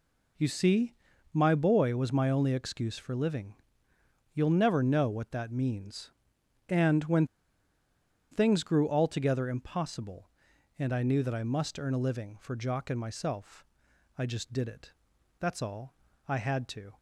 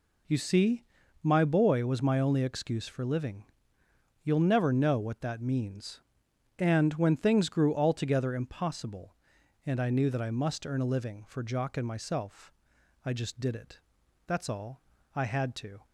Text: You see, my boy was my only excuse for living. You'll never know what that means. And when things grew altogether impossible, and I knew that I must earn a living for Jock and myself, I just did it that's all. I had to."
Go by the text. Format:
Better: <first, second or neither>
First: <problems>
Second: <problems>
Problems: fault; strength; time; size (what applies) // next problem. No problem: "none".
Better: second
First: pauses between "when" and "things"; at 7.2 s; 1.0 s long // pauses between "it" and "that's"; noticeable; at 14.9 s; 0.48 s long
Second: pauses between "it" and "that's"; noticeable; at 13.7 s; 0.48 s long